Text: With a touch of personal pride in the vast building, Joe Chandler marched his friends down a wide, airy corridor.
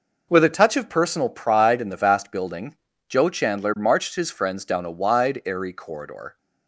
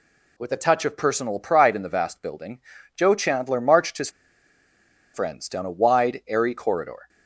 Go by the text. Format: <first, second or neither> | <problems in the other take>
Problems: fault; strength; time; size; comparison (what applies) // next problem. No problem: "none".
first | pauses between "his" and "friends"; at 4.1 s; 1.0 s long